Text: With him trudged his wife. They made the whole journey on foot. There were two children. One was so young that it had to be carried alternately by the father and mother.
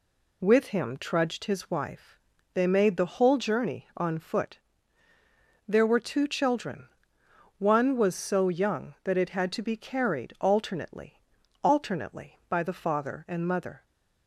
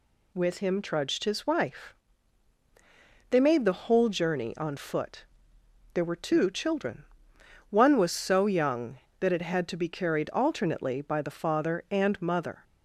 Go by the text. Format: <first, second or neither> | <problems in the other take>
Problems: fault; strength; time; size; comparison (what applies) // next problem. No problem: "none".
second | says "alternately" twice; at 11.6 s